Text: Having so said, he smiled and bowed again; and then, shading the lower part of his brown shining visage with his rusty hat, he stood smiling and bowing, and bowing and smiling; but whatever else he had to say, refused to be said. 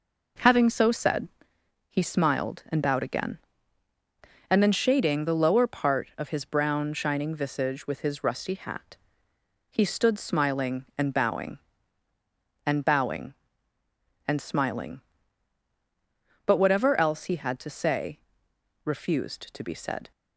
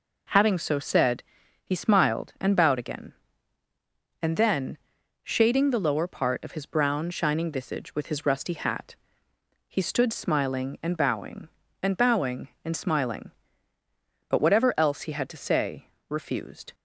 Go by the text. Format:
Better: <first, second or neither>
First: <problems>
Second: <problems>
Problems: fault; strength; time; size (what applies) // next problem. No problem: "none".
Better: first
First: none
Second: stops before "to be said"; at 16.7 s